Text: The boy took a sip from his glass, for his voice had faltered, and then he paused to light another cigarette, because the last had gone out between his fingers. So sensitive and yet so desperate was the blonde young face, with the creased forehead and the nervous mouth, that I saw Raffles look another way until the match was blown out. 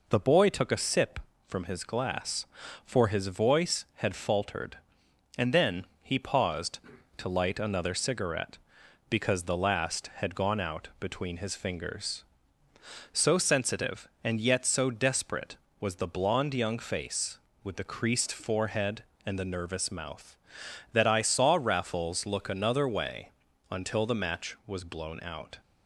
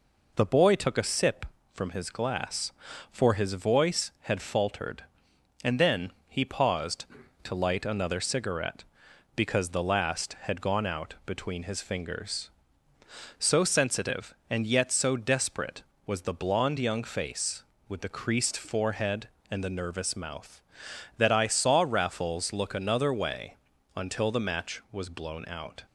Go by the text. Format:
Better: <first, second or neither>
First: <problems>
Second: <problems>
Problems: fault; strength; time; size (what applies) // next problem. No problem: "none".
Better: neither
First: pauses between "then" and "he"; slight; at 5.8 s; 0.16 s long // pauses between "way" and "until"; at 23.3 s; 0.40 s long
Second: pauses between "then" and "he"; slight; at 6.1 s; 0.16 s long // pauses between "way" and "until"; at 23.5 s; 0.40 s long